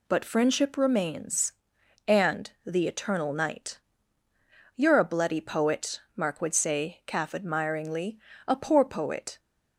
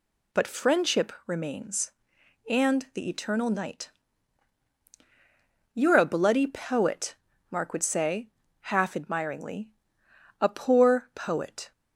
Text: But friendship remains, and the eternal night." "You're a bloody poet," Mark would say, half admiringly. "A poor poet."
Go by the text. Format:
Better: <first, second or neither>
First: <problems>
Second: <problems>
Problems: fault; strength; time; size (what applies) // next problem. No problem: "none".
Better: second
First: says "calf" for "half"; at 7.0 s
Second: none